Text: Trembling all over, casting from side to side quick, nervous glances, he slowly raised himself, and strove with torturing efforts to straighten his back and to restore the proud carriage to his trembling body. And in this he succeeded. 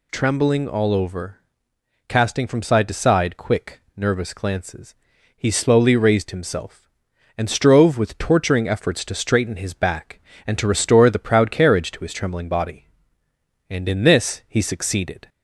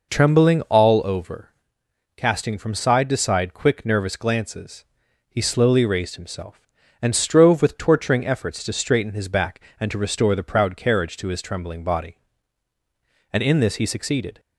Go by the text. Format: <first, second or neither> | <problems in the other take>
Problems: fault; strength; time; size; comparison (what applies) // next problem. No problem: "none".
neither | none